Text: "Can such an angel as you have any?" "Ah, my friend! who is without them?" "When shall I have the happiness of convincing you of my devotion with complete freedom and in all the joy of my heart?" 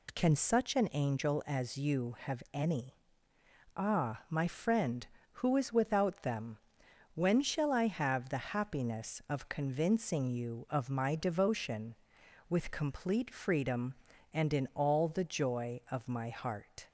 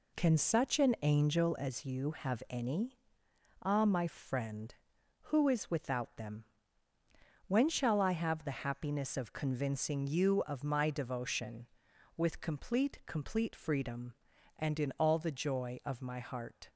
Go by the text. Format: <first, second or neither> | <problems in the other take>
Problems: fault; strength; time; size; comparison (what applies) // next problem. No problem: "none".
first | says "complete" twice; at 13.0 s